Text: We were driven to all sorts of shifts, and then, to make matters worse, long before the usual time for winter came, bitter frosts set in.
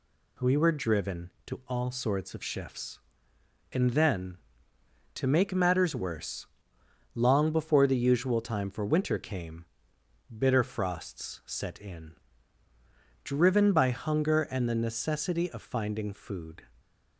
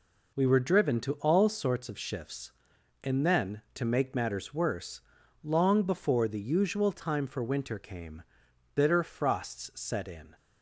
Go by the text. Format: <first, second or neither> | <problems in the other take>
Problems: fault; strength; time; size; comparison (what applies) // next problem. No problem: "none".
second | goes on to say "Driven by hunger and the necessity of finding food"; strong; from 13.2 s on; 3.4 s long